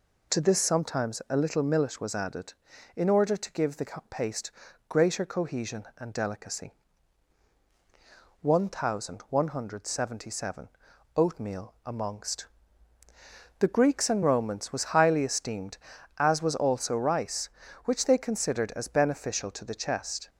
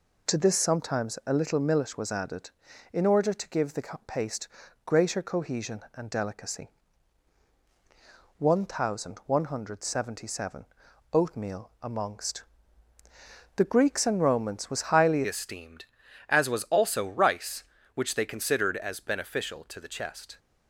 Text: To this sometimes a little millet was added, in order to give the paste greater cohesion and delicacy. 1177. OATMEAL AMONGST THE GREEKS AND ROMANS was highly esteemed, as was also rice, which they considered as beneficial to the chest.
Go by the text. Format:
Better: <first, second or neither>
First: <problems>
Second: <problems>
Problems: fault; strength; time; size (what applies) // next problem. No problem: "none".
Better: first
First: pauses between "the" and "paste"; slight; at 3.8 s; 0.24 s long // pauses between "paste" and "greater"; slight; at 4.5 s; 0.36 s long // pauses between "AMONGST" and "THE"; at 12.4 s; 1.1 s long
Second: pauses between "the" and "paste"; slight; at 3.8 s; 0.24 s long // pauses between "paste" and "greater"; slight; at 4.4 s; 0.36 s long // pauses between "AMONGST" and "THE"; at 12.4 s; 1.1 s long // changes voice at "esteemed"; from 15.2 s on; 5.1 s long